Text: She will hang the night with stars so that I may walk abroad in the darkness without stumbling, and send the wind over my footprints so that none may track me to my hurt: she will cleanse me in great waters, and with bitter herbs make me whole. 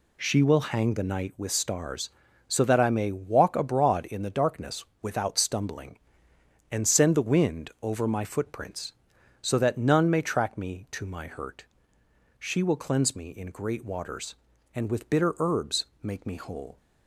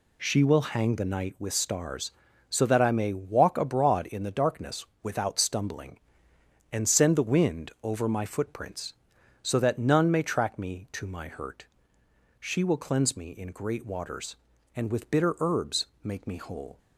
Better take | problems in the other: neither | pauses between "darkness" and "without"; slight; the same in both // pauses between "herbs" and "make"; slight; the same in both

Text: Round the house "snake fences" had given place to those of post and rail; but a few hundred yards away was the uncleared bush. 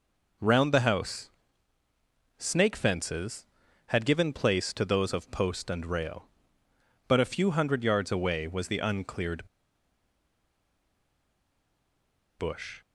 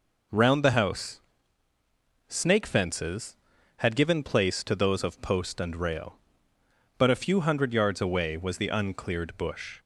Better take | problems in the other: second | pauses between "house" and "snake"; at 1.2 s; 1.0 s long; also in the second // pauses between "uncleared" and "bush"; strong; at 9.4 s; 2.9 s long

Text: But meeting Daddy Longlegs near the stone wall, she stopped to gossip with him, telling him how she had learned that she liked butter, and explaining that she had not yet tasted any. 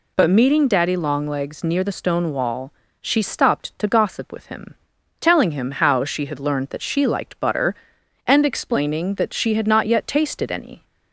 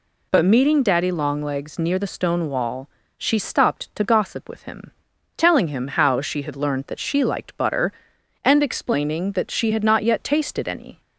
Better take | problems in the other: neither | none

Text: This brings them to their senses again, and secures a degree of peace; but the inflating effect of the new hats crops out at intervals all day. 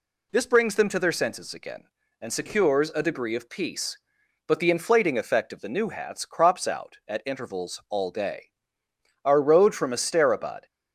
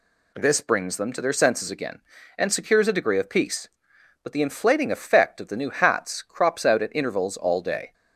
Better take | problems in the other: second | goes on to say "Our road from Asterabad"; from 9.2 s on; 1.4 s long

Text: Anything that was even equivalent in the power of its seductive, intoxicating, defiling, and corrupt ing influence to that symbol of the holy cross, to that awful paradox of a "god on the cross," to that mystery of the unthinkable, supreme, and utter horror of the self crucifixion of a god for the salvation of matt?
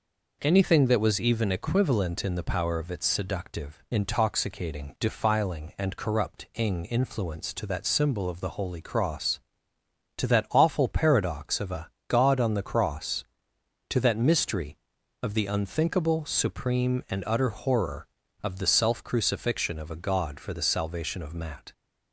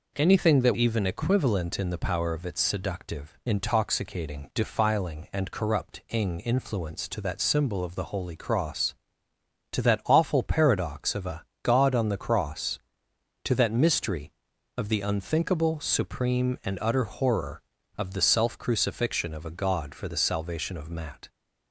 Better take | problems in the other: first | skips "was"; at 0.7 s // pauses between "a" and "god"; slight; at 11.4 s; 0.18 s long; slight in the first

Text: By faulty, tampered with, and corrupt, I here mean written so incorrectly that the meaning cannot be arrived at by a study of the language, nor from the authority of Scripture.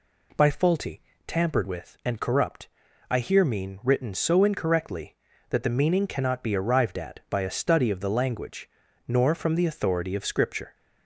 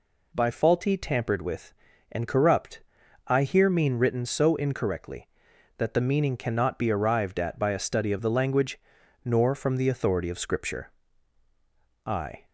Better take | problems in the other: first | goes on to say "I"; slight; from 12.0 s on; 0.40 s long

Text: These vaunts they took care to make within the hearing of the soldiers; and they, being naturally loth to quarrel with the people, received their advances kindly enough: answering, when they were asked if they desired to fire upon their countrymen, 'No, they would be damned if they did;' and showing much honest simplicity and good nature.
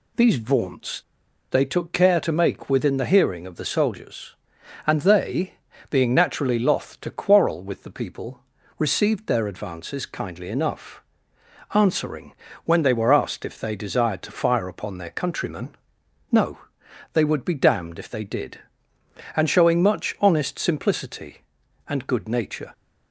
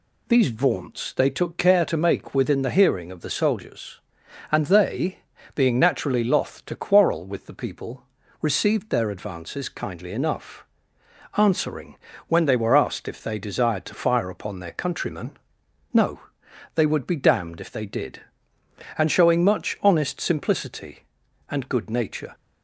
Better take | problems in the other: second | pauses between "vaunts" and "they"; noticeable; at 0.9 s; 0.51 s long

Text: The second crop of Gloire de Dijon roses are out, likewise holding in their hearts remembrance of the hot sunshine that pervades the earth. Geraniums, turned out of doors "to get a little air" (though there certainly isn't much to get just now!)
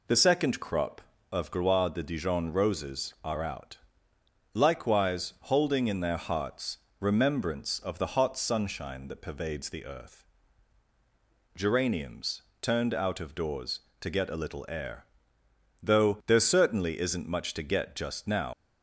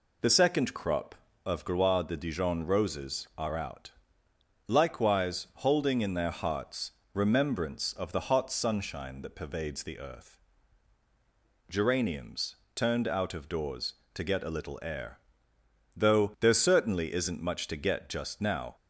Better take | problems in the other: second | pauses between "hearts" and "remembrance"; slight; at 6.7 s; 0.22 s long; slight in the second // leaves "now" unfinished; at 18.5 s; 85 ms

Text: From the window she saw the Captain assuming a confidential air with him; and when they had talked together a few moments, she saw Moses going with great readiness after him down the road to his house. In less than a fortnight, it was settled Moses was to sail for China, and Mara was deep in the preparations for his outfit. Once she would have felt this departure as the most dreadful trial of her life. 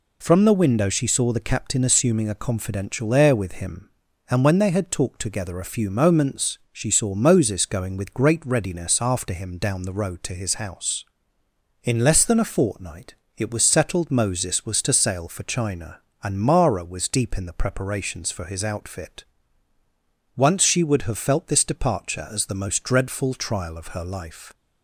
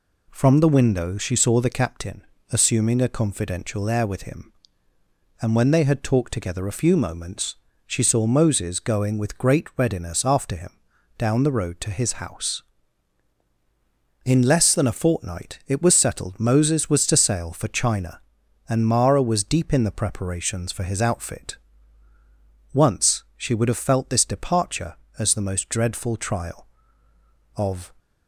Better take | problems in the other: first | pauses between "Captain" and "assuming"; slight; at 2.2 s; 0.26 s long // pauses between "him" and "down"; noticeable; at 10.7 s; 0.48 s long // stops before "her life"; at 27.9 s

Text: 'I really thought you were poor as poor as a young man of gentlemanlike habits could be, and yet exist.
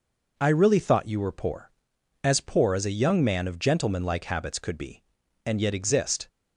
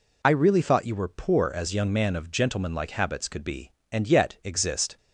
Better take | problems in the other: first | skips "poor as a"; at 1.7 s

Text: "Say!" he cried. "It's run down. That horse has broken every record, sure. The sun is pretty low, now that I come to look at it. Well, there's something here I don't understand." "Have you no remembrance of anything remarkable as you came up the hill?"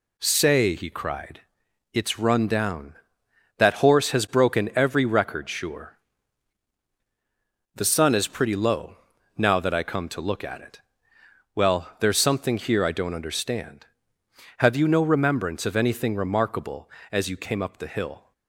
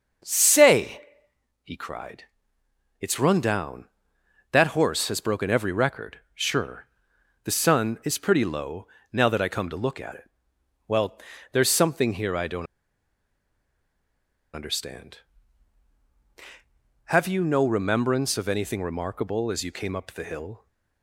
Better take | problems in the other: first | starts louder than the rest; until 1.8 s; 6.5 dB // pauses between "don't" and "understand"; strong; at 12.6 s; 1.8 s long

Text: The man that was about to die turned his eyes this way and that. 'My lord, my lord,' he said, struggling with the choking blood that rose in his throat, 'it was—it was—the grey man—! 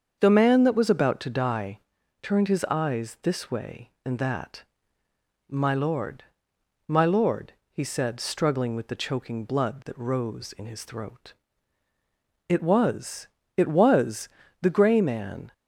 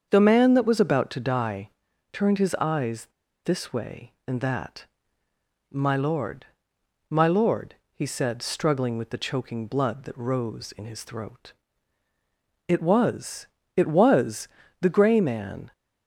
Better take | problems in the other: first | starts louder than the rest; until 1.1 s; 7 dB; also in the first // pauses between "die" and "turned"; noticeable; at 1.6 s; 0.46 s long; noticeable in the first // pauses between "eyes" and "this"; at 3.0 s; 0.36 s long

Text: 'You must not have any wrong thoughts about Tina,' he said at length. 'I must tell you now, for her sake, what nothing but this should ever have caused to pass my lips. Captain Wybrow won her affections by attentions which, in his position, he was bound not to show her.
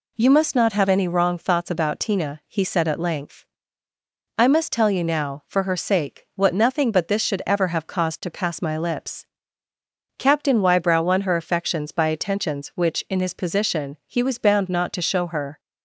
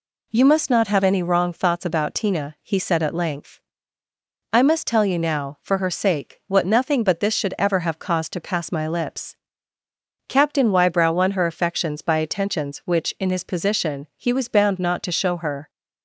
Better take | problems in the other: neither | none

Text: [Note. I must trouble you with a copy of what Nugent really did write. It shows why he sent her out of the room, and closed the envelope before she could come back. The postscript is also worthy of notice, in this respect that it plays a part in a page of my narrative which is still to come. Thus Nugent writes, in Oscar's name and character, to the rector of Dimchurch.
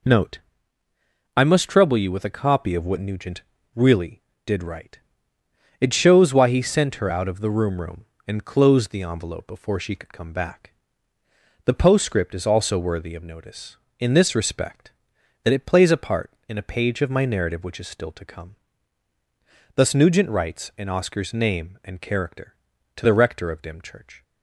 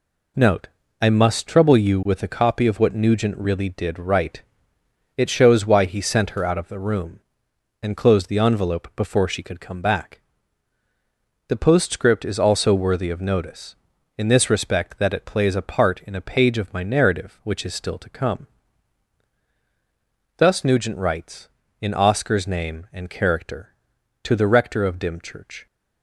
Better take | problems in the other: second | pauses between "Nugent" and "really"; slight; at 3.4 s; 0.30 s long // says "room" twice; at 7.7 s

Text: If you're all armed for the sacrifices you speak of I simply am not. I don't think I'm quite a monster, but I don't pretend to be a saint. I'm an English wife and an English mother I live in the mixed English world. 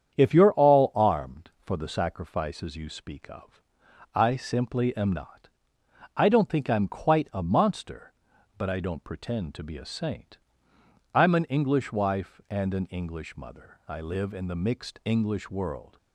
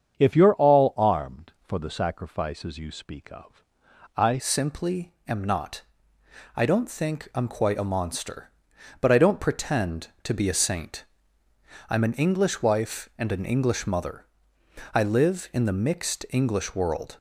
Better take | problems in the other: first | starts louder than the rest; strong; until 1.2 s; 7.5 dB; strong in the first // pauses between "of" and "I"; noticeable; at 3.6 s; 0.50 s long; noticeable in the first // changes voice at "simply"; from 4.3 s on; 12.8 s long // pauses between "simply" and "am"; slight; at 5.1 s; 0.16 s long // pauses between "mother" and "I"; noticeable; at 14.2 s; 0.68 s long

